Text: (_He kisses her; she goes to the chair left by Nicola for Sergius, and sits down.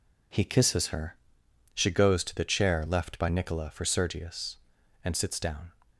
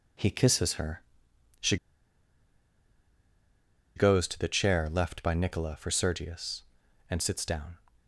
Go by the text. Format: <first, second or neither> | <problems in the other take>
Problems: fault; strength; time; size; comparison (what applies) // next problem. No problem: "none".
first | pauses between "she" and "goes"; strong; at 1.7 s; 2.1 s long